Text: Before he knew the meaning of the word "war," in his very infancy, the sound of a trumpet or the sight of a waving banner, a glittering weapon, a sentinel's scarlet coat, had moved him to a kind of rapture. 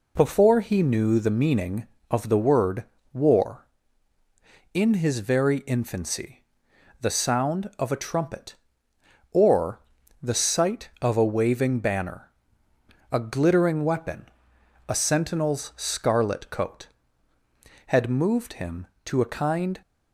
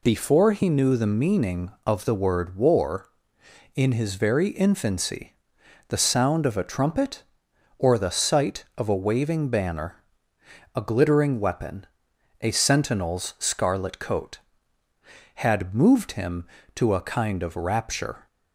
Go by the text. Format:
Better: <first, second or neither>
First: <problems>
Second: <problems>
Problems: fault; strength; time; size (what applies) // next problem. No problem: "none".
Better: second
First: pauses between "word" and "war"; slight; at 2.8 s; 0.28 s long // pauses between "or" and "the"; at 9.8 s; 0.40 s long // stops before "of rapture"; at 19.8 s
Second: none